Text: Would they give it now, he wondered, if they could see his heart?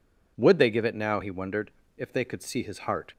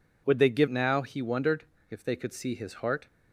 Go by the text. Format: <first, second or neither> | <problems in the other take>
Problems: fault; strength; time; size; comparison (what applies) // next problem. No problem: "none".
first | skips "it"; at 0.6 s